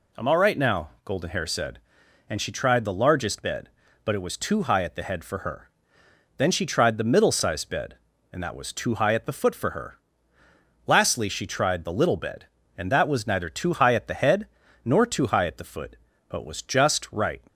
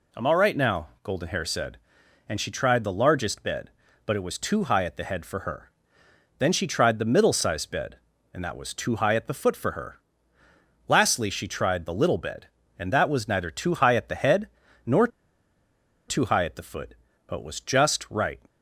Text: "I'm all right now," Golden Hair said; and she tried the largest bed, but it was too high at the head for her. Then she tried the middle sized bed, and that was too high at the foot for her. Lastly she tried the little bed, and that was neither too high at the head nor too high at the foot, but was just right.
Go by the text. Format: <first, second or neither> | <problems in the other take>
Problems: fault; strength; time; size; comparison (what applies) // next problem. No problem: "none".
first | pauses between "head" and "nor"; slight; at 14.4 s; 0.36 s long; slight in the first // pauses between "nor" and "too"; at 15.0 s; 1.0 s long